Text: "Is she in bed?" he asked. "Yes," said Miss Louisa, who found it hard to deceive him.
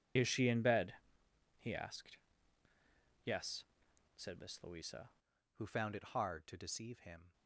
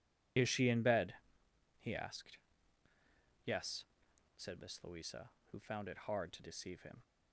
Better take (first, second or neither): second